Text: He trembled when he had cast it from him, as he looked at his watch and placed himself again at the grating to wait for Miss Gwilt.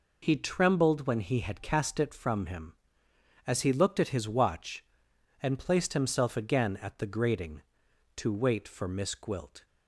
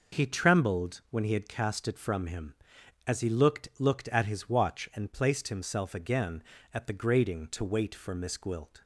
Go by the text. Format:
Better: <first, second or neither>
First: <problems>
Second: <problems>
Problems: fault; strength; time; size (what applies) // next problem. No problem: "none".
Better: first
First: none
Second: says "looked" twice; at 3.7 s